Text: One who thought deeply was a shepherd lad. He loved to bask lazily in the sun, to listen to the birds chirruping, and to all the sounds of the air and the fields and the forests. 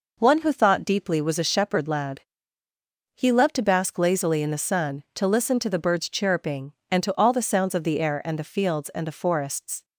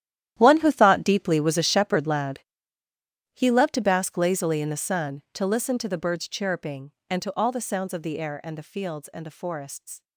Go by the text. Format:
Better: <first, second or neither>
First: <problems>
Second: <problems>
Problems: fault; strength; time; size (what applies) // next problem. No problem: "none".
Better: first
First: none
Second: gets quieter; strong; throughout; 15.5 dB